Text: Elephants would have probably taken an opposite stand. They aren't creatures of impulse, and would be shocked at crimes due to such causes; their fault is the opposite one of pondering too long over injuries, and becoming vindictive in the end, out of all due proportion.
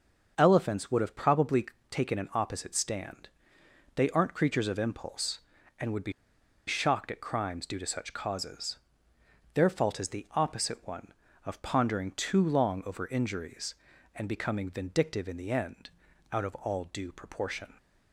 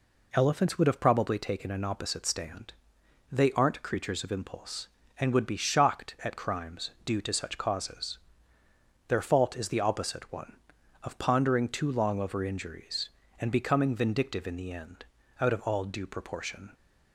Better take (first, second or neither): second